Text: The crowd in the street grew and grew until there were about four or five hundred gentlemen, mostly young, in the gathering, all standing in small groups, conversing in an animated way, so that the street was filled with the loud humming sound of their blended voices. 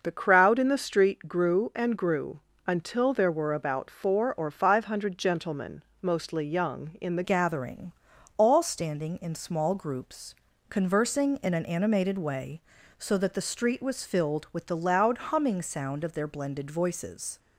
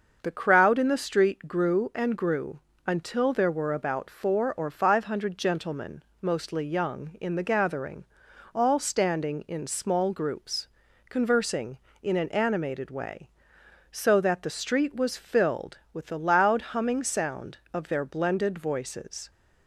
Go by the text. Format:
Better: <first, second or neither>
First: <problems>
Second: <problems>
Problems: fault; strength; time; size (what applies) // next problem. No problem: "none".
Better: second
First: starts louder than the rest; noticeable; until 1.0 s; 6 dB // pauses between "grew" and "until"; slight; at 2.4 s; 0.26 s long // changes voice at "gathering"; from 7.2 s on; 10.1 s long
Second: starts louder than the rest; until 1.2 s; 6.5 dB // pauses between "grew" and "until"; slight; at 2.5 s; 0.26 s long